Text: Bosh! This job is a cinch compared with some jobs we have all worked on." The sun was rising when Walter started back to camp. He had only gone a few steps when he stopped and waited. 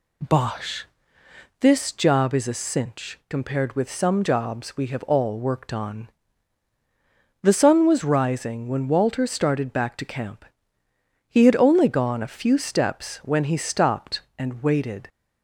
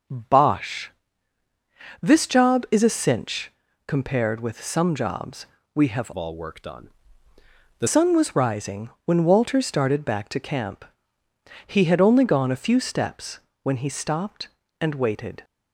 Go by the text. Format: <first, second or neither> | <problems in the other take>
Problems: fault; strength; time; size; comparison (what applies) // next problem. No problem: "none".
first | pauses between "cinch" and "compared"; slight; at 3.5 s; 0.36 s long // pauses between "jobs" and "we"; slight; at 5.4 s; 0.26 s long // changes voice from "all" to "The"; from 6.1 to 7.8 s; 1.7 s long // pauses between "rising" and "when"; slight; at 8.8 s; 0.16 s long // pauses between "steps" and "when"; slight; at 13.3 s; 0.24 s long